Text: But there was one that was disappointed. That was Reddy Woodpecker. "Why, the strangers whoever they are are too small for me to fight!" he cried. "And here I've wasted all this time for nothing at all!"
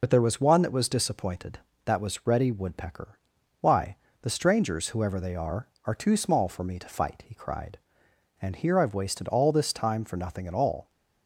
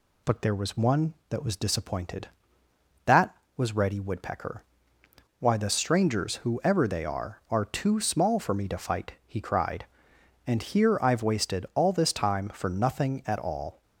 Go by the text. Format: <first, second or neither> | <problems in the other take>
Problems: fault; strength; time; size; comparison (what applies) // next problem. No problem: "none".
second | loses the start of "But"; at 0.0 s; 45 ms